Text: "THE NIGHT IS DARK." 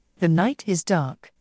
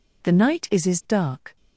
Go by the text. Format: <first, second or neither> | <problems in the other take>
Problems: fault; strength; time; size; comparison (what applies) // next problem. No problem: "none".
first | says "IS" twice; at 0.8 s